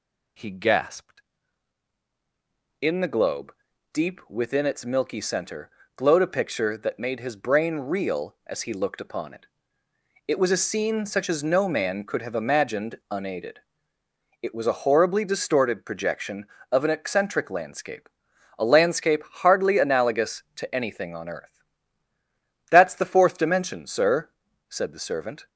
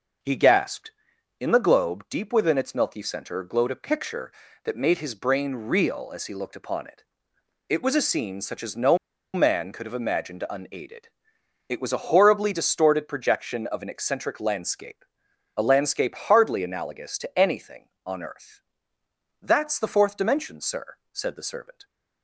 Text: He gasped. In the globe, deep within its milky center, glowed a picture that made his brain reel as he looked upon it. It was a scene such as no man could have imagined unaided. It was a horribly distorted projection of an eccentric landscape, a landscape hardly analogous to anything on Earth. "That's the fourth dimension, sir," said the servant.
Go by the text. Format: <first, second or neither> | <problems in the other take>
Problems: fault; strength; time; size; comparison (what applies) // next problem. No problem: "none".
first | pauses between "no" and "man"; at 8.9 s; 0.37 s long